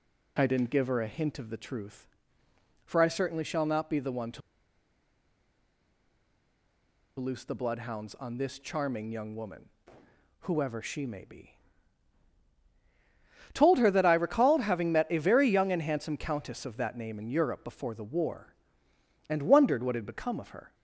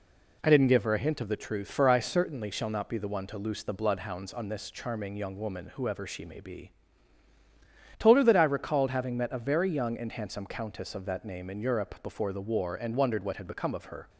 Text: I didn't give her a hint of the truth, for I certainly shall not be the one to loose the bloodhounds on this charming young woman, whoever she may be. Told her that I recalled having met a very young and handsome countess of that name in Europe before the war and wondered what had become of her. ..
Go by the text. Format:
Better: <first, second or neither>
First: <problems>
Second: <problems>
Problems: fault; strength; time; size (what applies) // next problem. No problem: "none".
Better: second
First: pauses between "to" and "loose"; strong; at 4.4 s; 2.7 s long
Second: none